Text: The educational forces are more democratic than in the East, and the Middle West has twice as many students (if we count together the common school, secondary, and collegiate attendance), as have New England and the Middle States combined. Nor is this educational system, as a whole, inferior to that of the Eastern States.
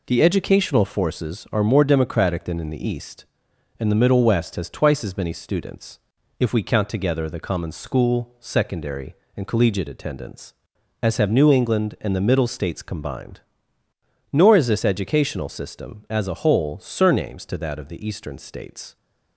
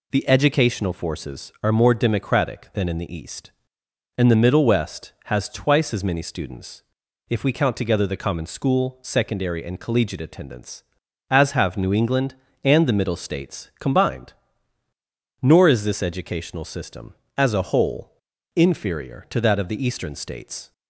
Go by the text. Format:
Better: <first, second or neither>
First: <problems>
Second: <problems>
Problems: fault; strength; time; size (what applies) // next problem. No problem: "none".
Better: second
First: says "surnames" for "inferior"; at 16.8 s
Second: none